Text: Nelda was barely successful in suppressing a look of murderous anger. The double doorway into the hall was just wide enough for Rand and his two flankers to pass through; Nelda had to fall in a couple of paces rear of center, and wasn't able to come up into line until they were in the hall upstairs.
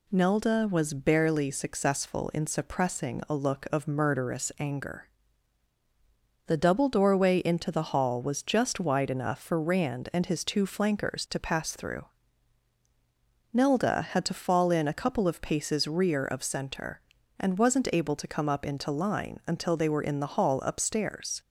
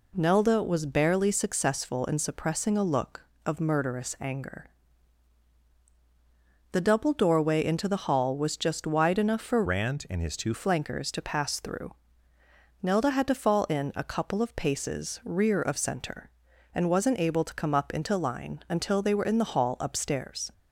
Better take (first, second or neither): first